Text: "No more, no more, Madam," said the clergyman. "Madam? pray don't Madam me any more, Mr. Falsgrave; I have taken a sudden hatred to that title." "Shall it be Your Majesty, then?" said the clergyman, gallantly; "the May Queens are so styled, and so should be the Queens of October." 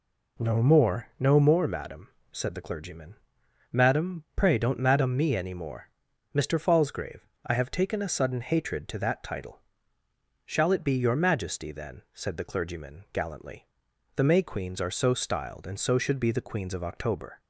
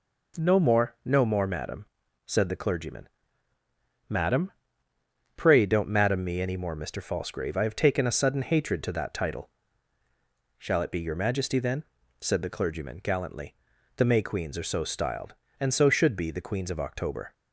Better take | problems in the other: neither | none

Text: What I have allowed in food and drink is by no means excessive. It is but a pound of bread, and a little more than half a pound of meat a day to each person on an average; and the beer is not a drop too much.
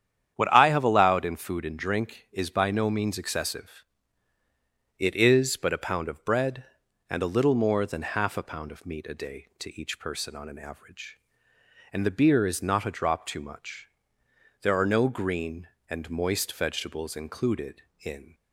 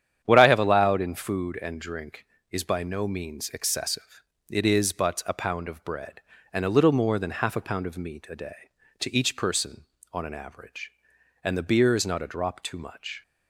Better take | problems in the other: second | starts louder than the rest; strong; until 1.3 s; 9 dB; strong in the second // goes on to say "There are no green and moist vegetables included in"; strong; from 14.6 s on; 3.7 s long

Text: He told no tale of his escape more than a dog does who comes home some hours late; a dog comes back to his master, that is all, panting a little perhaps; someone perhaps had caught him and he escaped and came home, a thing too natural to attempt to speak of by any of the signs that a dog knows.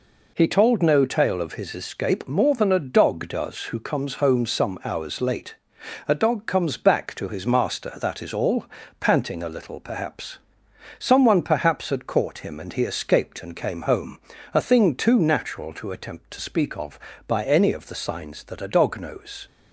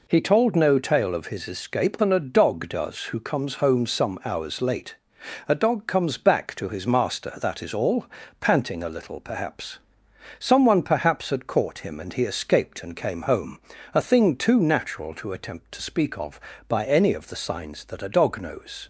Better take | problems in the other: first | skips "more"; at 1.9 s

